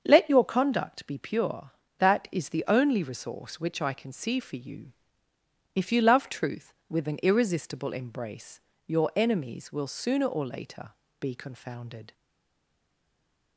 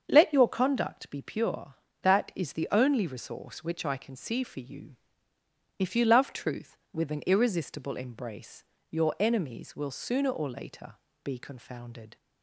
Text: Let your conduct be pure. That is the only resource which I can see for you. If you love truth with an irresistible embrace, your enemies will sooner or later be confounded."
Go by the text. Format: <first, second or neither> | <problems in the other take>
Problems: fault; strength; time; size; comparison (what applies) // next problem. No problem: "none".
second | starts louder than the rest; until 1.0 s; 7 dB; also in the second // pauses between "later" and "be"; slight; at 10.8 s; 0.30 s long; slight in the second // stays silent after the last word; noticeable; from 12.1 s on; 1.4 s long